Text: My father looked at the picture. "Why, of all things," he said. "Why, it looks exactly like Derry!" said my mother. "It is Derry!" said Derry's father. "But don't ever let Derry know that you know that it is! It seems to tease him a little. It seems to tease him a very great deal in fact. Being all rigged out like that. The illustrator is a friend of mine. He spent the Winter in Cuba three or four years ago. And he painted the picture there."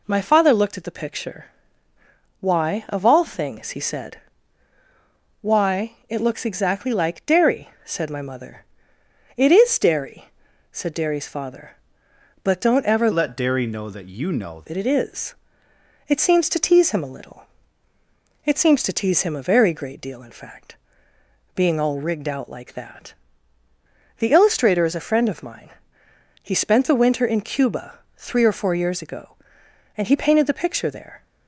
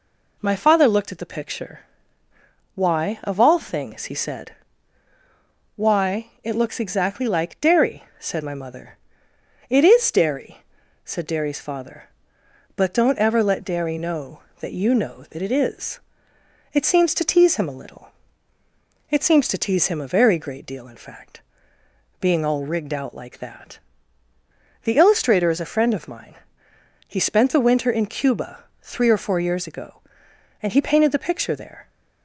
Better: second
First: changes voice from "let" to "know"; from 13.1 to 14.6 s; 1.5 s long // pauses between "Cuba" and "three"; slight; at 28.0 s; 0.16 s long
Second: pauses between "Cuba" and "three"; slight; at 28.6 s; 0.16 s long

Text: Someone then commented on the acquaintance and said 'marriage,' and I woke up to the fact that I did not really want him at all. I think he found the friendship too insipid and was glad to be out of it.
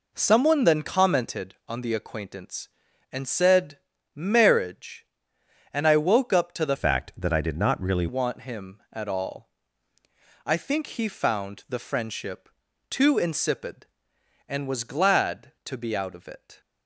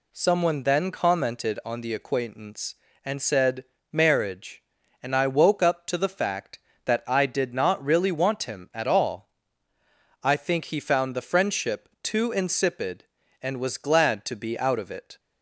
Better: second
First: pauses between "said" and "marriage"; slight; at 3.8 s; 0.34 s long // changes voice from "fact" to "really"; from 6.7 to 8.0 s; 1.3 s long // pauses between "friendship" and "too"; at 12.5 s; 0.40 s long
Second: pauses between "said" and "marriage"; slight; at 3.6 s; 0.28 s long

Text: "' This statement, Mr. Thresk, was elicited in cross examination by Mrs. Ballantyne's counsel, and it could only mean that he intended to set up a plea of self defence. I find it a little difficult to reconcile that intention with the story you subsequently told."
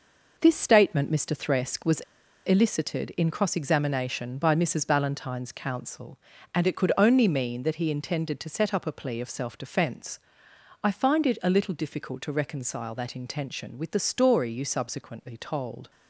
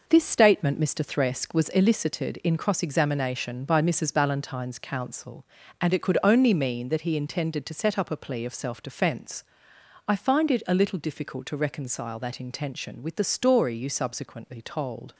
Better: second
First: pauses between "was" and "elicited"; noticeable; at 1.9 s; 0.48 s long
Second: none

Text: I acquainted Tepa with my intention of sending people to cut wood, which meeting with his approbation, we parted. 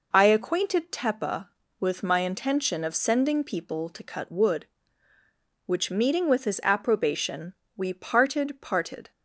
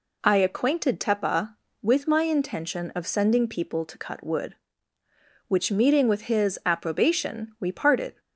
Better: second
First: says "parted" twice; at 8.6 s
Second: none

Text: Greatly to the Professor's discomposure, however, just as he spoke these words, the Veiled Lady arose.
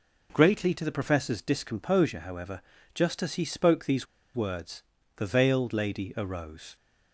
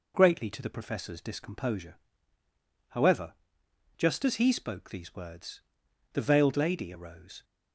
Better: second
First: pauses between "these" and "words"; slight; at 4.0 s; 0.29 s long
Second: none

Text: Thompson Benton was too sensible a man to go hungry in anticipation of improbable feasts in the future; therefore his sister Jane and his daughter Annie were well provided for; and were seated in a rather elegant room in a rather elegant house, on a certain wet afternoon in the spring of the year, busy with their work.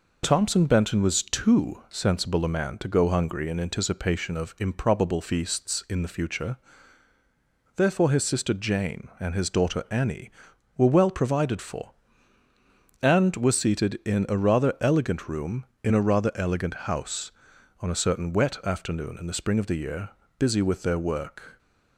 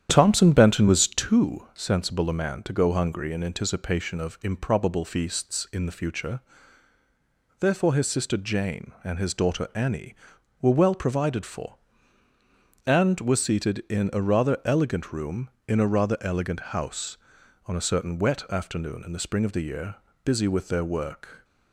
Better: first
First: none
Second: starts louder than the rest; strong; until 1.3 s; 9.5 dB

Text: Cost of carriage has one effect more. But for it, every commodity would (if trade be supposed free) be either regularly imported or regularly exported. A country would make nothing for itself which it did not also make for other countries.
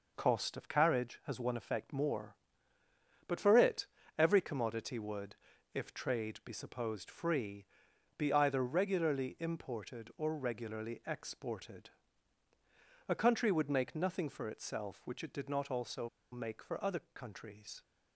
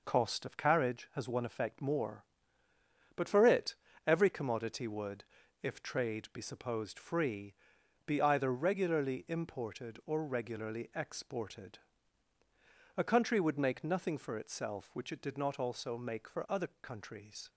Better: second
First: pauses between "also" and "make"; slight; at 16.0 s; 0.24 s long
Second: none

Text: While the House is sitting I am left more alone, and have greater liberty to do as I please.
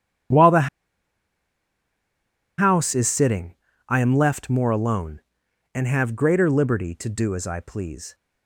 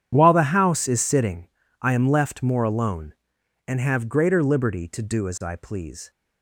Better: second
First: starts louder than the rest; strong; until 3.2 s; 9.5 dB // pauses between "the" and "House"; strong; at 0.6 s; 1.9 s long // pauses between "sitting" and "I"; slight; at 3.5 s; 0.34 s long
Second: starts louder than the rest; strong; until 1.1 s; 9.5 dB // pauses between "sitting" and "I"; slight; at 1.4 s; 0.34 s long

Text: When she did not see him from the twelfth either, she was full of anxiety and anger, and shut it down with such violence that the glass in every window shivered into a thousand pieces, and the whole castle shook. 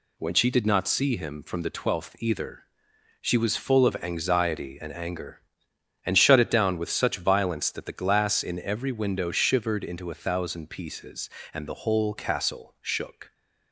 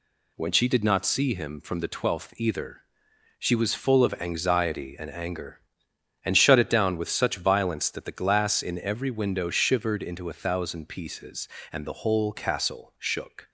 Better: neither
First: none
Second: none

